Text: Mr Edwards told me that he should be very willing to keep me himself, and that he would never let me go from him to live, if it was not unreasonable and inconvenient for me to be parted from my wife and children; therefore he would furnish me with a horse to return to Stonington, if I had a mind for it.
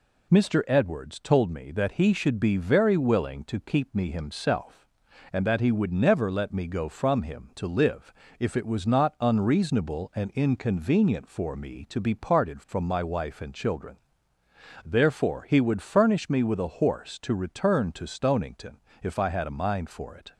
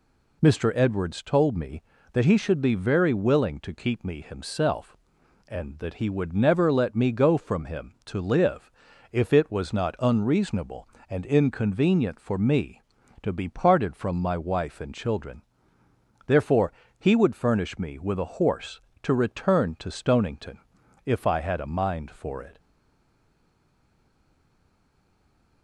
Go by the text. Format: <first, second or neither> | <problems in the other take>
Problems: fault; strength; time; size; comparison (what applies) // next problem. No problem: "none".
first | pauses between "therefore" and "he"; slight; at 16.7 s; 0.26 s long // stays silent after the last word; strong; from 22.5 s on; 3.1 s long